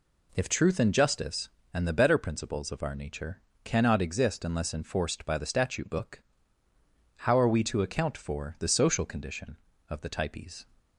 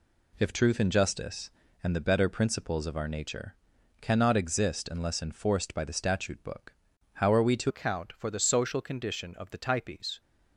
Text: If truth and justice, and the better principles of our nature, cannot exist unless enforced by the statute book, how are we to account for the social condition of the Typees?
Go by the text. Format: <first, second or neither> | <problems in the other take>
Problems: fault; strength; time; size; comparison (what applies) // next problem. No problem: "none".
first | changes voice at "account"; from 7.6 s on; 2.5 s long